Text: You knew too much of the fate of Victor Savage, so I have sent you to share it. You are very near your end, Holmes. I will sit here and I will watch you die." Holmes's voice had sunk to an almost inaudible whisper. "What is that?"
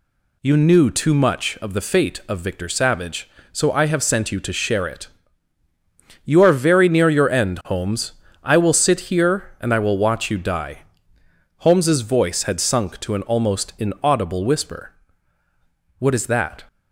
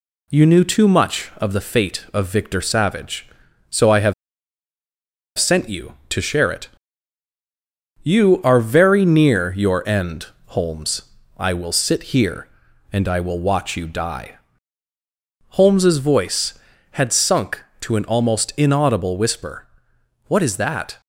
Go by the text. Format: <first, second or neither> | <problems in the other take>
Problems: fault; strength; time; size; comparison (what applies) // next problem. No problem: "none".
first | pauses between "have" and "sent"; strong; at 4.1 s; 1.2 s long